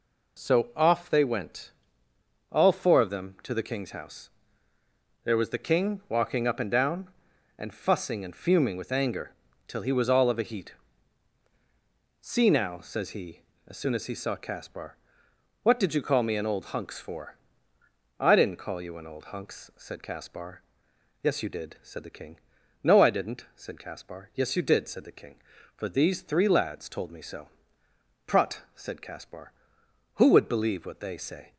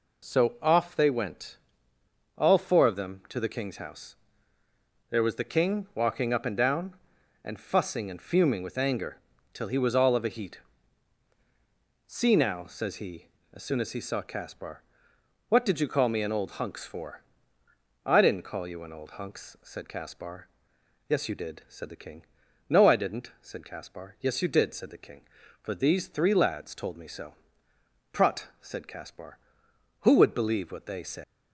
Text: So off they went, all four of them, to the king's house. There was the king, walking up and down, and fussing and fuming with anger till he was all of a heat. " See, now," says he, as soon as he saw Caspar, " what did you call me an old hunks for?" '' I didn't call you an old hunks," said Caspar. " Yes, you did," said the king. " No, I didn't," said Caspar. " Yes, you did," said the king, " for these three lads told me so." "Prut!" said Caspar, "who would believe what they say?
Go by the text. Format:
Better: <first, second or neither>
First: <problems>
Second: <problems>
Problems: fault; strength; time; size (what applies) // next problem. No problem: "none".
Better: first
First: pauses between "anger" and "till"; slight; at 9.3 s; 0.34 s long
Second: pauses between "anger" and "till"; slight; at 9.1 s; 0.34 s long // leaves "say" unfinished; at 31.2 s; 155 ms